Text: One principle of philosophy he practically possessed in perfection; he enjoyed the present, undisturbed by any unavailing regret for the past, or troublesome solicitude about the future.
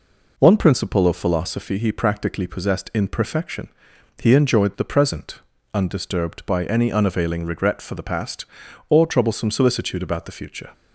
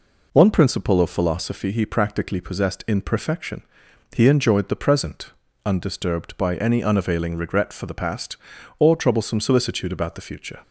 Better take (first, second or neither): neither